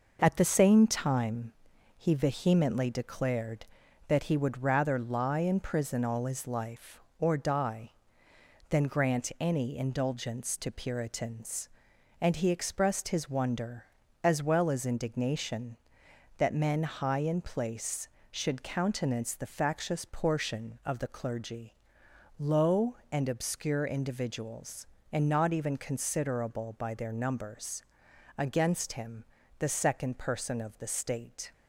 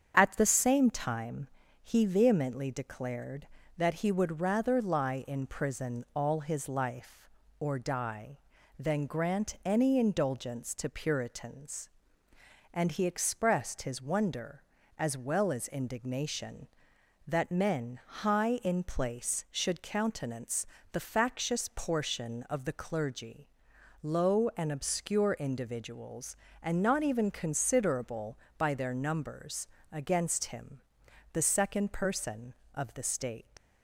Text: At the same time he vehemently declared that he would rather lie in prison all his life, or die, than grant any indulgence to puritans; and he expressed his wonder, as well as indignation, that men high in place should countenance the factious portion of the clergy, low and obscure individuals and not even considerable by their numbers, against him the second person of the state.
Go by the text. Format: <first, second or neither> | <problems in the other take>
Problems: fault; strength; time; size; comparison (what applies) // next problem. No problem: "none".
first | starts louder than the rest; strong; until 1.1 s; 7 dB // pauses between "time" and "he"; slight; at 1.4 s; 0.36 s long; also in the first // pauses between "countenance" and "the"; slight; at 20.6 s; 0.28 s long // pauses between "him" and "the"; noticeable; at 30.7 s; 0.52 s long; slight in the first // leaves "state" unfinished; at 33.5 s; 125 ms